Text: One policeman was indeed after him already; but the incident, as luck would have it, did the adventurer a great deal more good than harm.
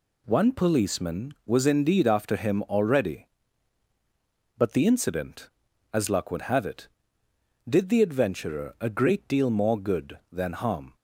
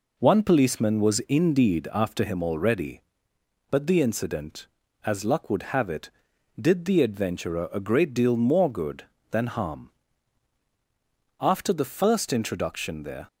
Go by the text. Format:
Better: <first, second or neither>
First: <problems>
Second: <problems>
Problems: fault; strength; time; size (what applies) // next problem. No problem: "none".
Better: first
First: none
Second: goes on to say "After the first introduction there"; strong; from 11.4 s on; 1.8 s long